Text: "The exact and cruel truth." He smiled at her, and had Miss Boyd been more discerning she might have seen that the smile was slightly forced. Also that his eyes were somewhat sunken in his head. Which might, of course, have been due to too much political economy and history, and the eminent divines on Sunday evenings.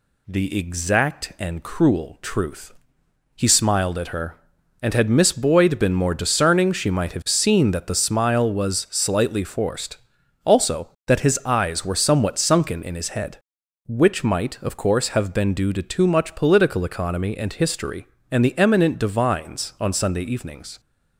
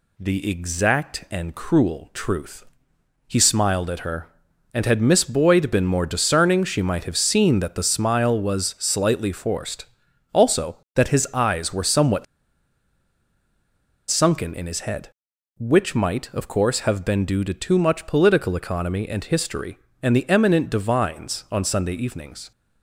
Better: first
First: none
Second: pauses between "somewhat" and "sunken"; strong; at 12.2 s; 1.8 s long

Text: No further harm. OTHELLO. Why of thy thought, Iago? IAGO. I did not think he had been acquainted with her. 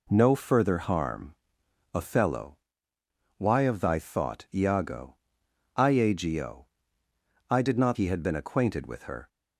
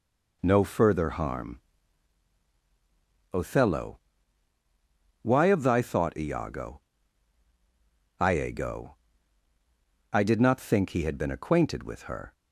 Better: second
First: skips "think"; at 7.9 s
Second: none

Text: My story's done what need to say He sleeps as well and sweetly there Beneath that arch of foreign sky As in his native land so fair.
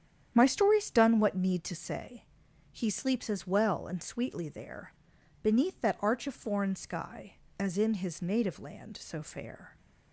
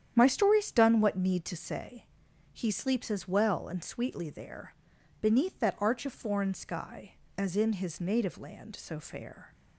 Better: neither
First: starts louder than the rest; strong; until 1.3 s; 9.5 dB // pauses between "say" and "He"; noticeable; at 2.2 s; 0.48 s long // pauses between "there" and "Beneath"; noticeable; at 4.9 s; 0.50 s long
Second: starts louder than the rest; strong; until 1.1 s; 9.5 dB // pauses between "say" and "He"; noticeable; at 2.0 s; 0.48 s long // pauses between "there" and "Beneath"; noticeable; at 4.7 s; 0.48 s long

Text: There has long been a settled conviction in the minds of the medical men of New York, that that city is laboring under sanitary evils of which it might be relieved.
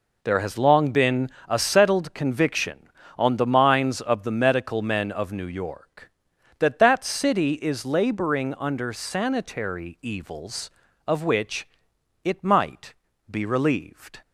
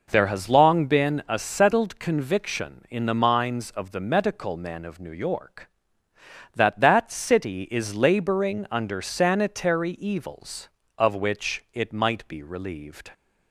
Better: second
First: pauses between "been" and "a"; slight; at 1.3 s; 0.18 s long // says "on" for "in"; at 3.1 s // pauses between "which" and "it"; noticeable; at 11.6 s; 0.56 s long // pauses between "might" and "be"; slight; at 12.9 s; 0.36 s long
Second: none

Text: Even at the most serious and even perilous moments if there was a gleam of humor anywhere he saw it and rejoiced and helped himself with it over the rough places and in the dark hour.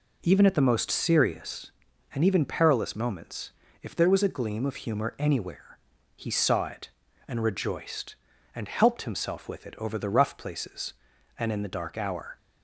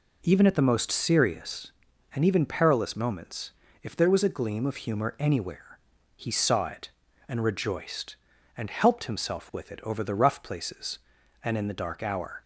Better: neither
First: pauses between "moments" and "if"; slight; at 3.4 s; 0.32 s long // pauses between "anywhere" and "he"; slight; at 5.7 s; 0.36 s long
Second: pauses between "moments" and "if"; slight; at 3.4 s; 0.32 s long // pauses between "anywhere" and "he"; slight; at 5.7 s; 0.36 s long

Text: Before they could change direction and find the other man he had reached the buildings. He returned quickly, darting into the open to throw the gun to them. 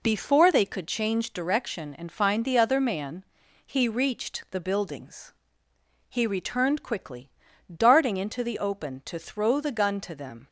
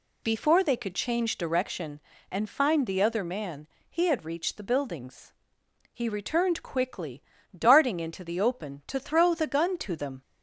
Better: second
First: pauses between "man" and "he"; at 3.2 s; 0.40 s long // skips "had"; at 3.8 s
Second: pauses between "man" and "he"; slight; at 3.6 s; 0.22 s long

